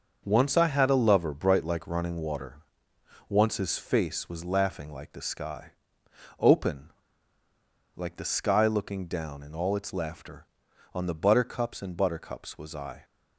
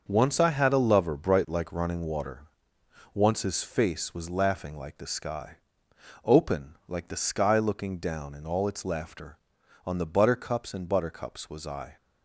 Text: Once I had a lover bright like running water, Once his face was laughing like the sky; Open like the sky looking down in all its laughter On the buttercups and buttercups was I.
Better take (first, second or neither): second